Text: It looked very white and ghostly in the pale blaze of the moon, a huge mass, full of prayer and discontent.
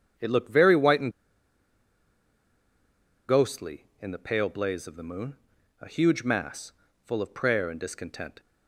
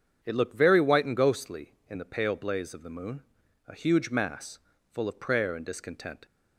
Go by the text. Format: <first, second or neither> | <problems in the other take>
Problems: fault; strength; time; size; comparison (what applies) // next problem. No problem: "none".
second | starts louder than the rest; strong; until 3.3 s; 7.5 dB; strong in the second // pauses between "and" and "ghostly"; strong; at 1.1 s; 2.1 s long